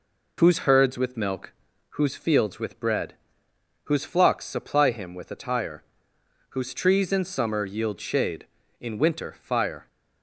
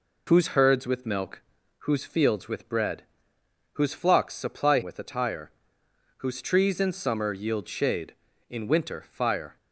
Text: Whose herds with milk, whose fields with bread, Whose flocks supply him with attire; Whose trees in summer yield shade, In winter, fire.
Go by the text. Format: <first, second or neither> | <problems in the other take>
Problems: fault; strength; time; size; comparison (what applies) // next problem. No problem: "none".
first | skips "him"; at 4.8 s